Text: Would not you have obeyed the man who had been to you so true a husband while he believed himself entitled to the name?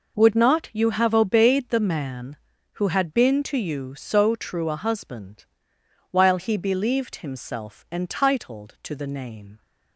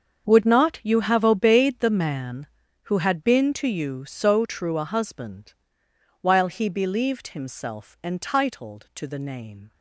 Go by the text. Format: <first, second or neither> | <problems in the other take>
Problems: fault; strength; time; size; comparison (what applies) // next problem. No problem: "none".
first | gets quieter; strong; throughout; 15.5 dB // pauses between "husband" and "while"; noticeable; at 5.5 s; 0.70 s long; noticeable in the first